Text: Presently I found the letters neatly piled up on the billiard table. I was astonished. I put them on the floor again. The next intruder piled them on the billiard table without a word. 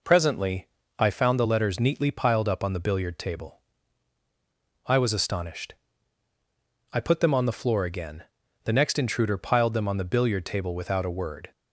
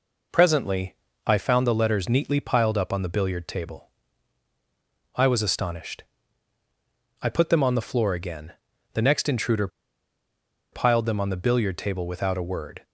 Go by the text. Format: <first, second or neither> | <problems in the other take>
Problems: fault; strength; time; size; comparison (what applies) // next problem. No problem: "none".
first | pauses between "Presently" and "I"; slight; at 0.9 s; 0.30 s long; slight in the first // pauses between "intruder" and "piled"; at 9.6 s; 1.0 s long